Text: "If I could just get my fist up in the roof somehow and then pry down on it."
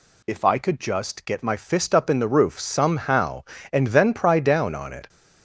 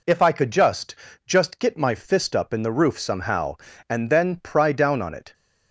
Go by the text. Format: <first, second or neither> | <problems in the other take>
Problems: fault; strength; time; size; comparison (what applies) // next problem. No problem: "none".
first | says "just" twice; at 1.2 s